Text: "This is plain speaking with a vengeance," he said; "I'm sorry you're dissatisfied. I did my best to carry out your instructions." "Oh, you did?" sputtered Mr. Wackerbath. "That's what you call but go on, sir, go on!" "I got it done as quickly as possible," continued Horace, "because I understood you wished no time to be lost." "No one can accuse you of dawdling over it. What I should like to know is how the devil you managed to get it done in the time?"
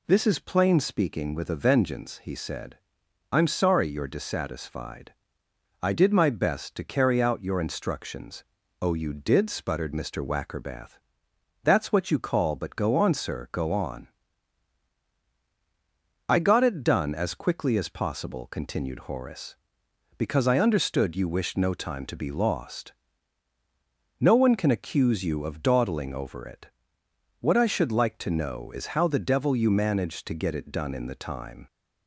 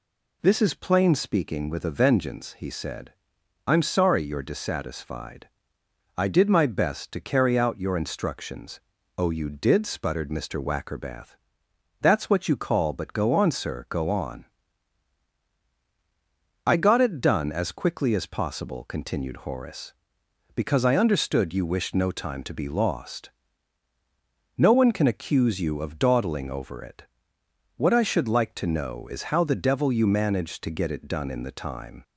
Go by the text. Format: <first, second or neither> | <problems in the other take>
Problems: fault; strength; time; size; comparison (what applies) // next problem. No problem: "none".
neither | none